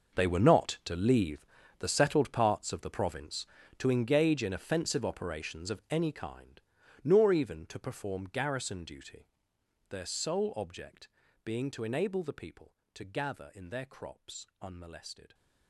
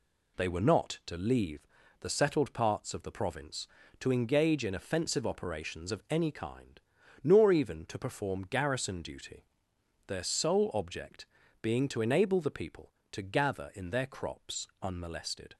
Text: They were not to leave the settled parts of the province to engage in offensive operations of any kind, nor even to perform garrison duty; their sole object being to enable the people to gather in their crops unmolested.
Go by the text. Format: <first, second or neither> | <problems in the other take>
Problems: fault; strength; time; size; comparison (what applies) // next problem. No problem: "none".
second | gets quieter; strong; throughout; 16.5 dB // pauses between "leave" and "the"; slight; at 1.4 s; 0.34 s long; slight in the second // pauses between "object" and "being"; slight; at 11.0 s; 0.36 s long; slight in the second